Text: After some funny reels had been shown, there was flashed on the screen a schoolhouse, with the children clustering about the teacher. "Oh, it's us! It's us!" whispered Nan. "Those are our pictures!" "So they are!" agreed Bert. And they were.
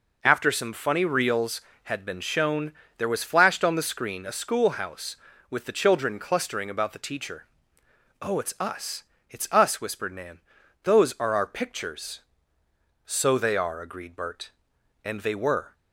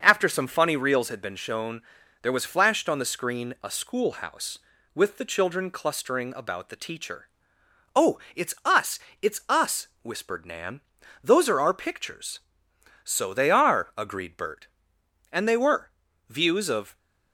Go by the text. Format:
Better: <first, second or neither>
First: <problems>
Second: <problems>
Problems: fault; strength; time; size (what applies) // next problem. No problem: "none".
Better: first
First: none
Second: starts louder than the rest; until 1.0 s; 6.5 dB // goes on to say "Views of"; noticeable; from 16.2 s on; 0.70 s long